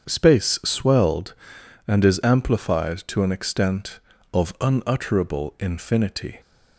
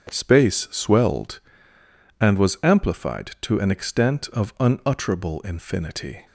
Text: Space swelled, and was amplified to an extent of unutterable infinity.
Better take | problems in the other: second | starts louder than the rest; strong; until 1.1 s; 7.5 dB; strong in the second // says "is" for "was"; at 2.0 s

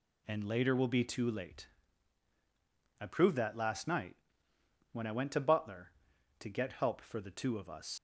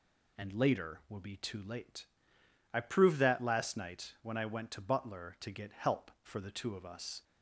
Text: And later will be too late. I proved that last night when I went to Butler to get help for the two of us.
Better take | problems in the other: second | pauses between "night" and "when"; noticeable; at 4.1 s; 0.76 s long // leaves "us" unfinished; at 7.9 s; 85 ms

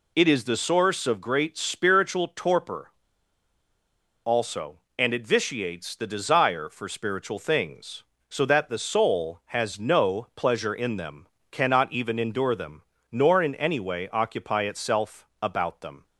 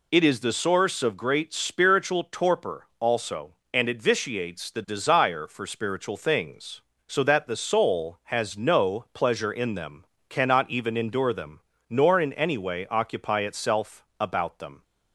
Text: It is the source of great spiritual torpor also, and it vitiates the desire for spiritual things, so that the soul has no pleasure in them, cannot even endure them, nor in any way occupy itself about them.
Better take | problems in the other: second | pauses between "torpor" and "also"; strong; at 2.8 s; 1.3 s long // pauses between "itself" and "about"; slight; at 15.2 s; 0.16 s long; slight in the second

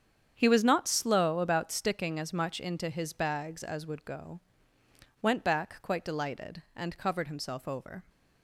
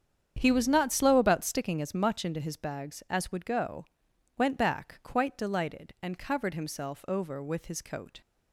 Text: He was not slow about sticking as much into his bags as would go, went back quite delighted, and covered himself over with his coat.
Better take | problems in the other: second | starts louder than the rest; strong; until 1.3 s; 8 dB; strong in the second // stops before "with his coat"; at 8.0 s

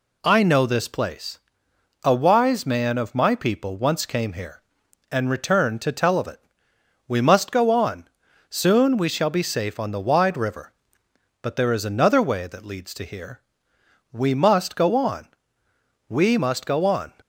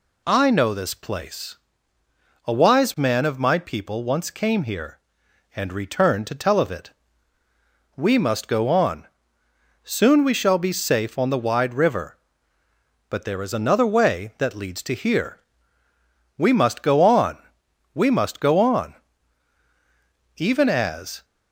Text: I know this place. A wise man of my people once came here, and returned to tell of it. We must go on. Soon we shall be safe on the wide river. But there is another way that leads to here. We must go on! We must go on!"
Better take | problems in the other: first | goes on to say "Even as"; noticeable; from 20.3 s on; 0.88 s long

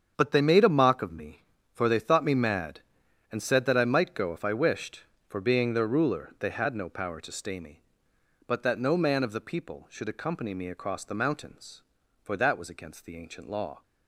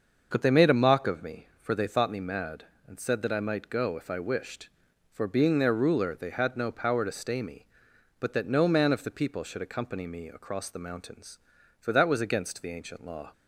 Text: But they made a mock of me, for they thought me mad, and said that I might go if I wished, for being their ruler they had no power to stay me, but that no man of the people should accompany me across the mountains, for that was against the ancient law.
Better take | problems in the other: neither | starts louder than the rest; the same in both

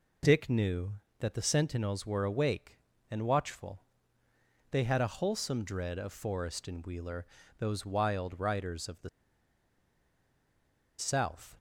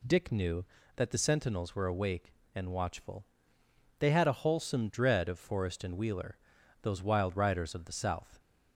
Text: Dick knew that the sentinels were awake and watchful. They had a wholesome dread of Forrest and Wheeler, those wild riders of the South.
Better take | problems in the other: second | pauses between "the" and "South"; strong; at 9.0 s; 1.8 s long

